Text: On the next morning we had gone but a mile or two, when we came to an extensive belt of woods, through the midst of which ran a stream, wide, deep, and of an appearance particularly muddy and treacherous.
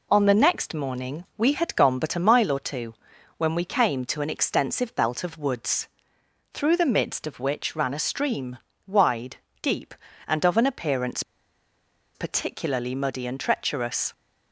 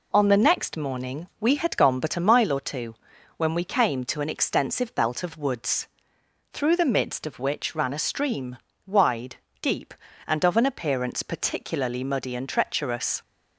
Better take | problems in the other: second | pauses between "appearance" and "particularly"; noticeable; at 11.2 s; 0.93 s long

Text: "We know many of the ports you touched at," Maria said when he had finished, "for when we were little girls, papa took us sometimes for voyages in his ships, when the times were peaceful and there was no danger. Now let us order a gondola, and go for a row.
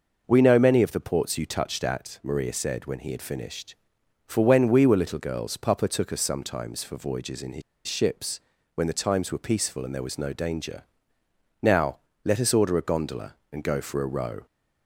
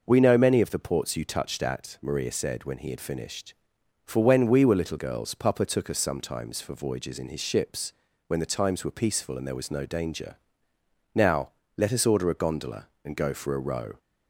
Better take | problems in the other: second | pauses between "his" and "ships"; slight; at 7.6 s; 0.25 s long // pauses between "Now" and "let"; slight; at 11.9 s; 0.26 s long; slight in the second

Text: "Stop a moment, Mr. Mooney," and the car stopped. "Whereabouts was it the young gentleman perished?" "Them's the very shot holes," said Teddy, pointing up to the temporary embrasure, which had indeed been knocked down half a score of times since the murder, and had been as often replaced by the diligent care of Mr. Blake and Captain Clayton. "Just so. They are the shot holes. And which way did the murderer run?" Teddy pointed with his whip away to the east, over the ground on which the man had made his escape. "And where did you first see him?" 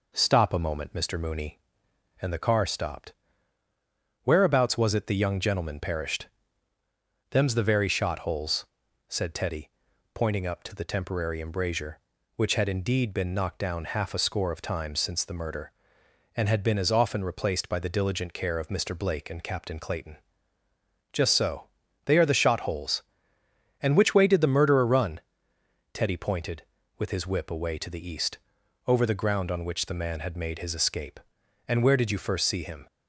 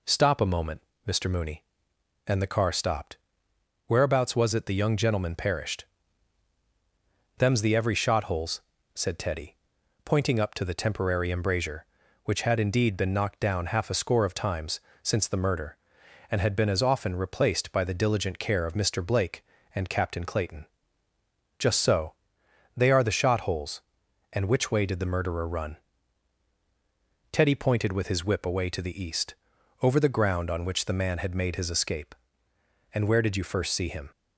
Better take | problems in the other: first | says "every" for "very"; at 7.7 s // pauses between "times" and "since"; slight; at 14.8 s; 0.22 s long

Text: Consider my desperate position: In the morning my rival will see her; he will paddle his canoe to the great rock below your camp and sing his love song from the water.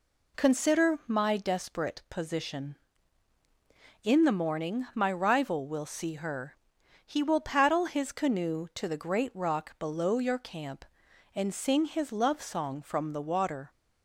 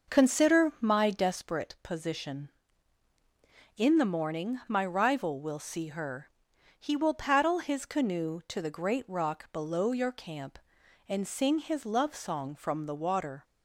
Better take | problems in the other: first | starts louder than the rest; noticeable; until 1.6 s; 5.5 dB

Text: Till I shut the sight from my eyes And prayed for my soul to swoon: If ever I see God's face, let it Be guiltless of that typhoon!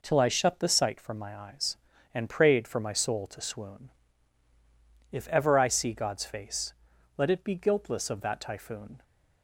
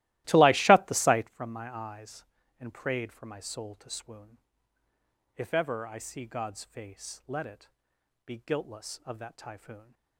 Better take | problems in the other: first | starts louder than the rest; strong; until 1.3 s; 16.5 dB // pauses between "it" and "Be"; noticeable; at 7.6 s; 0.58 s long

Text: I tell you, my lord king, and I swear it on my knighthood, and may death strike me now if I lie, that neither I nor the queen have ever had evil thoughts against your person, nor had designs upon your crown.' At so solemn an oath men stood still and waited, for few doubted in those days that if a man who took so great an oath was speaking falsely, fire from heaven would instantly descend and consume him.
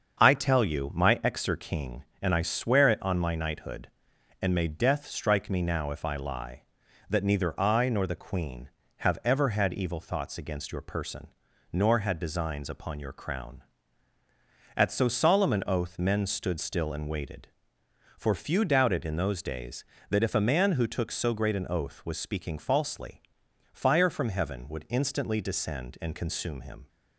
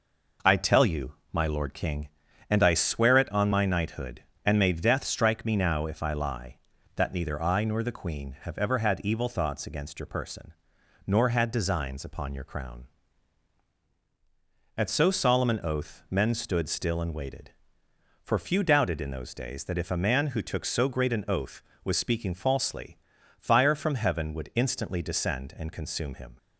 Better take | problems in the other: second | starts louder than the rest; until 1.2 s; 7 dB // says "exer" for "lord"; at 1.1 s

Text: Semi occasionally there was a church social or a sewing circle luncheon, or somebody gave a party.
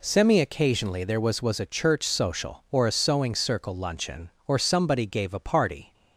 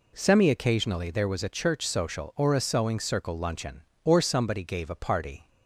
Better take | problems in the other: second | says "was" twice; at 1.4 s

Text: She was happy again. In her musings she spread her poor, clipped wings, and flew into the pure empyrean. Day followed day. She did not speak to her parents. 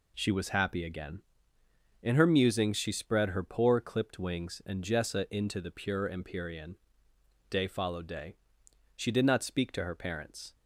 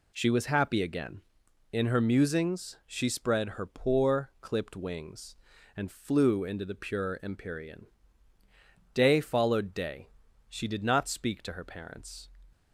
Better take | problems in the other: second | says "jessa" for "flew"; at 4.8 s

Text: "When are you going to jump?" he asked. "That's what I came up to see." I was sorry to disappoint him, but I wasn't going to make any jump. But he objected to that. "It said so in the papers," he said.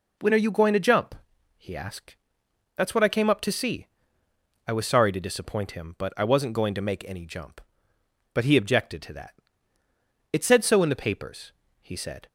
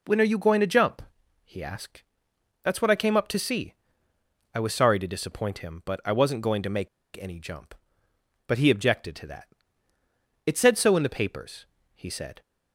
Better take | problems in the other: first | pauses between "make" and "any"; slight; at 6.8 s; 0.30 s long

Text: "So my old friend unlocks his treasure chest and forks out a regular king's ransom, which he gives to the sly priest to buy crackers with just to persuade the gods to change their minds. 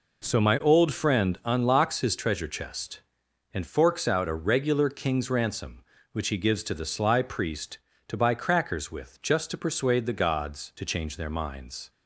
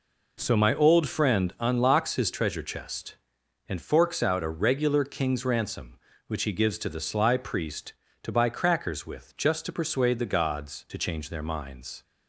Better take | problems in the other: neither | none

